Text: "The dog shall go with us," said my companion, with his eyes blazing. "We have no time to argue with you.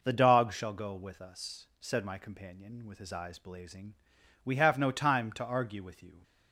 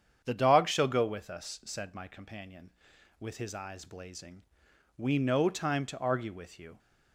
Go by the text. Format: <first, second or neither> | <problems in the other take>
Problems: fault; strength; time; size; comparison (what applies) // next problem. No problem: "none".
first | starts louder than the rest; strong; until 1.2 s; 8 dB // skips "have"; at 5.1 s